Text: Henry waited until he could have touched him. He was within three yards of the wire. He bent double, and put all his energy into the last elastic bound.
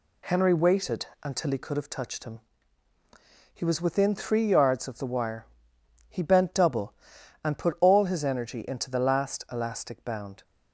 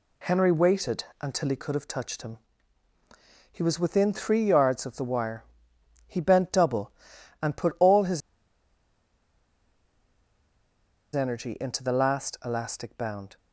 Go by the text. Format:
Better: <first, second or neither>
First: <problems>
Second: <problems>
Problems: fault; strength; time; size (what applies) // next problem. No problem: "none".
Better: first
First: pauses between "waited" and "until"; slight; at 1.0 s; 0.18 s long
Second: pauses between "waited" and "until"; slight; at 1.0 s; 0.18 s long // pauses between "his" and "energy"; strong; at 8.2 s; 2.9 s long